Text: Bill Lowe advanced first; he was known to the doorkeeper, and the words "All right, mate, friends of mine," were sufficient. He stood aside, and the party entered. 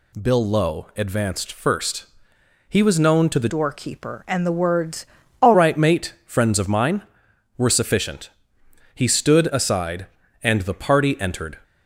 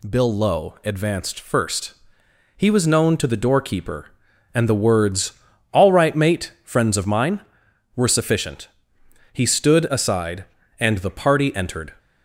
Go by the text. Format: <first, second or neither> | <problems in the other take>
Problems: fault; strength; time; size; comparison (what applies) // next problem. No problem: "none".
second | changes voice from "doorkeeper" to "All"; from 3.4 to 5.5 s; 2.1 s long // pauses between "words" and "All"; slight; at 5.0 s; 0.34 s long; also in the second